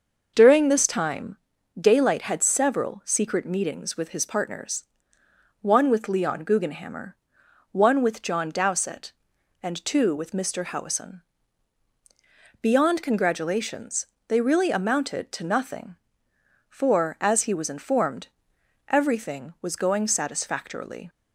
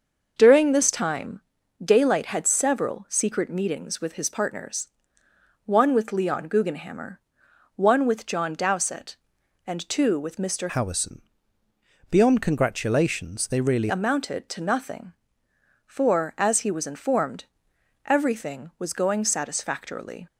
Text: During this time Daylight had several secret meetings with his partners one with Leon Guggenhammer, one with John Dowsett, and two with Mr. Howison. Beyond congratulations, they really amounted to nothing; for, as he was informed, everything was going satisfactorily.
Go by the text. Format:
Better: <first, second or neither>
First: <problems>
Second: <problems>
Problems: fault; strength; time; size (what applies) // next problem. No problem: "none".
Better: first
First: starts louder than the rest; noticeable; until 1.3 s; 6 dB // pauses between "time" and "Daylight"; at 1.3 s; 0.44 s long // pauses between "partners" and "one"; noticeable; at 4.8 s; 0.76 s long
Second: starts louder than the rest; noticeable; until 1.3 s; 6 dB // pauses between "time" and "Daylight"; at 1.4 s; 0.44 s long // pauses between "partners" and "one"; noticeable; at 4.8 s; 0.76 s long // changes voice from "Howison" to "really"; from 10.6 to 13.8 s; 3.2 s long